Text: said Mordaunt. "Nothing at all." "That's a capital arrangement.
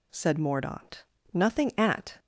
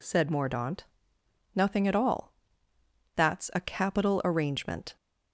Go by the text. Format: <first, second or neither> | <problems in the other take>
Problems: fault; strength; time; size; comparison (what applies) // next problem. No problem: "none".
second | stops before "all That's a capital arrangement"; at 2.1 s